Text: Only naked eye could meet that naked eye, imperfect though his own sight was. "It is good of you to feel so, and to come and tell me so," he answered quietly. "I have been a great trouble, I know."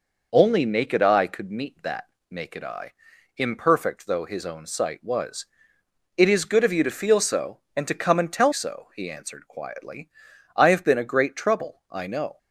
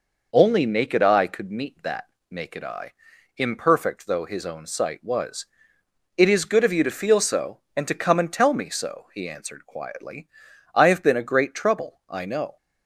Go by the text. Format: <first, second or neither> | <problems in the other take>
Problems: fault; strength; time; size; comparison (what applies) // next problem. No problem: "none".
second | pauses between "that" and "naked"; slight; at 2.0 s; 0.26 s long; slight in the second // skips "me"; at 8.5 s